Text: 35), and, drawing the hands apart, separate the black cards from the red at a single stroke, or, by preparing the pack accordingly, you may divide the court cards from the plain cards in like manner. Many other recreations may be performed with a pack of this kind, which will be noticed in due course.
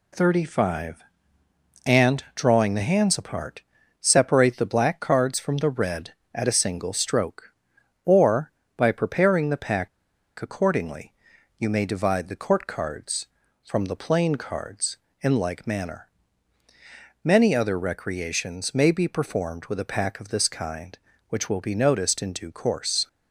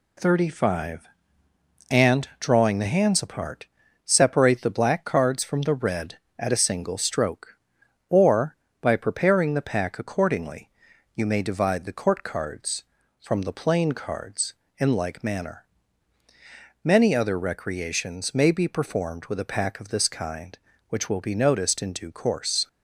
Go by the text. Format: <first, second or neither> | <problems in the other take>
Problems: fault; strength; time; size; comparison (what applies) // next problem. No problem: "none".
second | pauses between "pack" and "accordingly"; noticeable; at 9.8 s; 0.50 s long